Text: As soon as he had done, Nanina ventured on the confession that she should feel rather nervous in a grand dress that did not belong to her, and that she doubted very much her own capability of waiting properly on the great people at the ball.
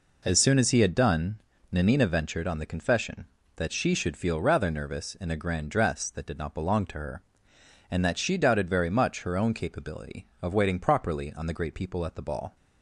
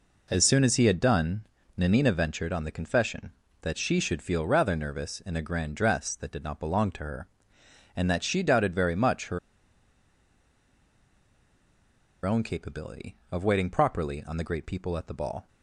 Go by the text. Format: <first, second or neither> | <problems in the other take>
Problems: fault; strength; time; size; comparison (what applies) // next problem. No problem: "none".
first | pauses between "her" and "own"; strong; at 9.3 s; 2.8 s long